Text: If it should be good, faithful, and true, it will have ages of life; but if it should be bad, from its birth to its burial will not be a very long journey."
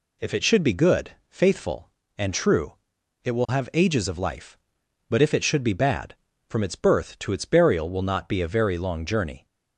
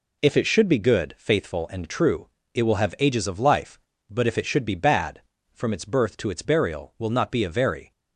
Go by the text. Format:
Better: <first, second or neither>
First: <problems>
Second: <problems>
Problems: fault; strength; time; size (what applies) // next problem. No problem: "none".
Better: first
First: none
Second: stops before "long journey"; at 7.9 s